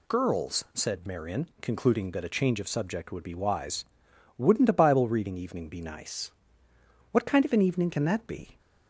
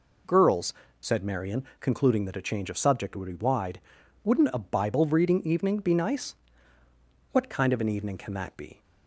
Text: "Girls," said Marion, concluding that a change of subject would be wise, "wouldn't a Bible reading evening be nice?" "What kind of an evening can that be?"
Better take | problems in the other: first | says "wide" for "wise"; at 3.4 s

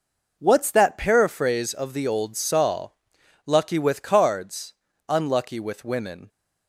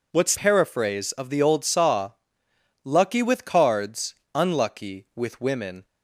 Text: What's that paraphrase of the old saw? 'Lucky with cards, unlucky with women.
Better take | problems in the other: first | skips "that"; at 0.3 s

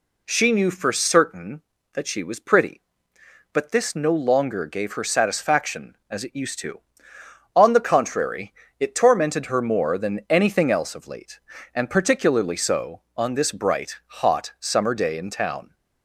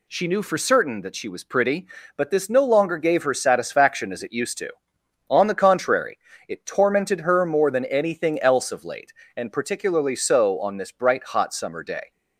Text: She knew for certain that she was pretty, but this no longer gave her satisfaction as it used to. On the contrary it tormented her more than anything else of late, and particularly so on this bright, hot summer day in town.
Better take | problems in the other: first | pauses between "contrary" and "it"; slight; at 6.1 s; 0.32 s long; slight in the first // stops before "in town"; at 12.1 s

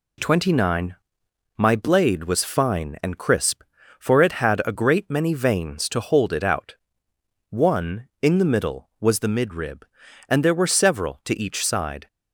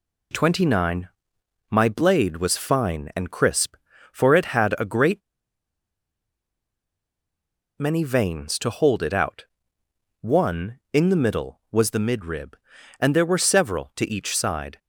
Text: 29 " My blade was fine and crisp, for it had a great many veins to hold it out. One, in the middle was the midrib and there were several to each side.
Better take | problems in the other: first | pauses between "great" and "many"; strong; at 5.2 s; 2.5 s long

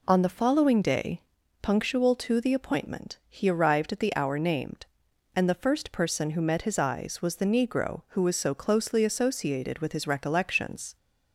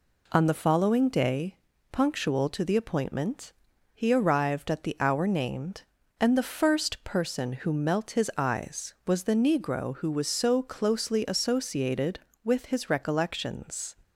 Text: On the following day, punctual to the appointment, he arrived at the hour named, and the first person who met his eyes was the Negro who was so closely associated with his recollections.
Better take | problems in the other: first | says "melt" for "met"; at 7.7 s

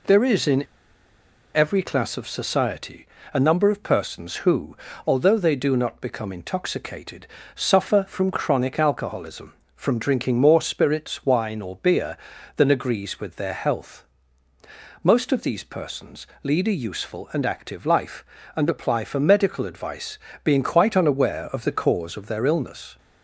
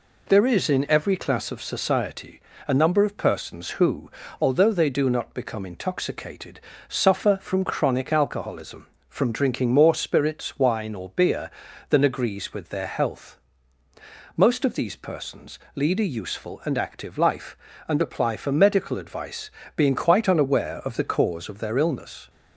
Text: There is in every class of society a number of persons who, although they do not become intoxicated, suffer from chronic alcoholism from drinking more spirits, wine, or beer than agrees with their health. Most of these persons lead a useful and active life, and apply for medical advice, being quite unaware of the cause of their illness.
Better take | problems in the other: second | pauses between "in" and "every"; noticeable; at 0.6 s; 0.91 s long // pauses between "society" and "a"; slight; at 3.0 s; 0.26 s long; slight in the second // pauses between "persons" and "lead"; slight; at 16.2 s; 0.16 s long; slight in the second

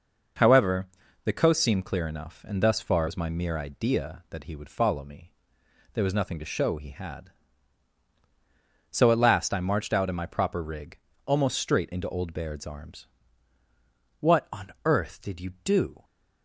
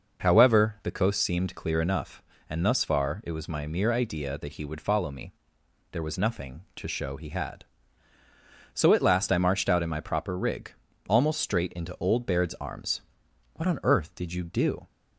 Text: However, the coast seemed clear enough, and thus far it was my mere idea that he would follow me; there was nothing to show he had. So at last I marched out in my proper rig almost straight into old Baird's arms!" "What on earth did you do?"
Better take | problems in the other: second | skips "it"; at 3.0 s // pauses between "rig" and "almost"; slight; at 10.9 s; 0.28 s long; slight in the second

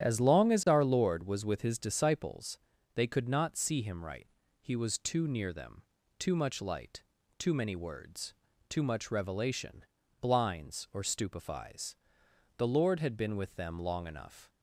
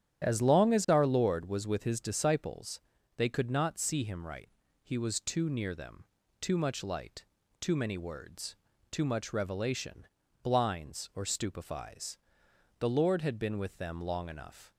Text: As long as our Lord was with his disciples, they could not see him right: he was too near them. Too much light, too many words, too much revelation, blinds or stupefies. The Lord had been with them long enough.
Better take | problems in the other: neither | starts louder than the rest; strong; the same in both

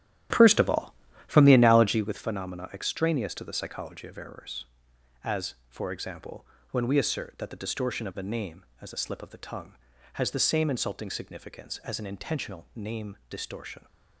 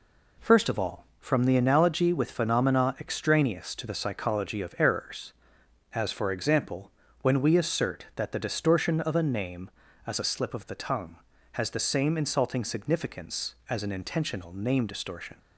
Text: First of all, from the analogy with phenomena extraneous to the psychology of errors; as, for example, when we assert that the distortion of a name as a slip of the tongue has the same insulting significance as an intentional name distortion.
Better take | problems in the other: second | starts louder than the rest; strong; until 2.2 s; 12 dB

